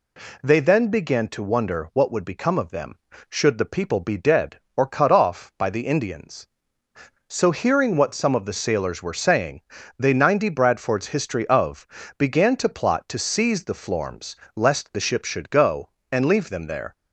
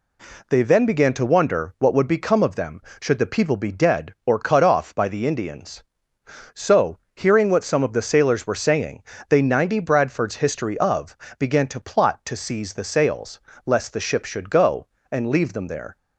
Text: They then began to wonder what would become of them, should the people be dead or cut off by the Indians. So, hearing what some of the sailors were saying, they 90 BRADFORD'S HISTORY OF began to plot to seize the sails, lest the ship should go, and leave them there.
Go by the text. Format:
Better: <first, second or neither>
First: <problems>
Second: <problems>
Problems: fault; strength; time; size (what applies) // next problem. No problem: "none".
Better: second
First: pauses between "OF" and "began"; slight; at 11.8 s; 0.32 s long // says "florms" for "sails"; at 13.7 s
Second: pauses between "OF" and "began"; slight; at 11.1 s; 0.22 s long